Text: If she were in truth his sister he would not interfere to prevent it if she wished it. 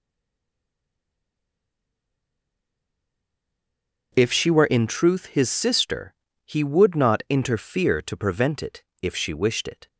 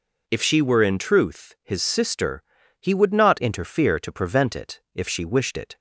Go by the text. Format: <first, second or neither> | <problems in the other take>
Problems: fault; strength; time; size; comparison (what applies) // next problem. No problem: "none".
second | stays silent before the first word; strong; until 4.1 s; 4.1 s long // starts louder than the rest; noticeable; until 5.1 s; 6 dB // pauses between "sister" and "he"; slight; at 6.1 s; 0.32 s long; also in the second // pauses between "it" and "if"; slight; at 8.8 s; 0.18 s long